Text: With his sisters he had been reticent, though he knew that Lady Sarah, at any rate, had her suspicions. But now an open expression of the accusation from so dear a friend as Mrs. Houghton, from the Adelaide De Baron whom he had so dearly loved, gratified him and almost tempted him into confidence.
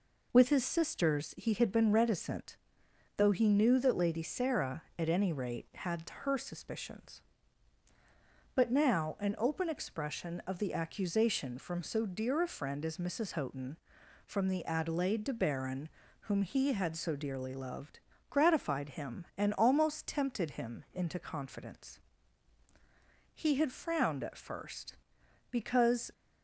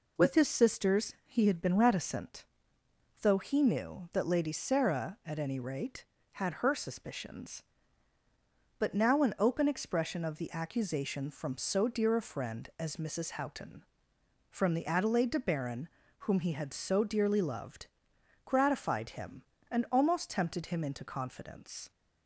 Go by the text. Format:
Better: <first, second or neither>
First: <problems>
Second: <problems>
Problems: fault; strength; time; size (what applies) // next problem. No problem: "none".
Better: second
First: pauses between "Baron" and "whom"; slight; at 15.8 s; 0.34 s long // goes on to say "He had frowned at first because"; strong; from 23.3 s on; 2.7 s long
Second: pauses between "Baron" and "whom"; slight; at 15.8 s; 0.34 s long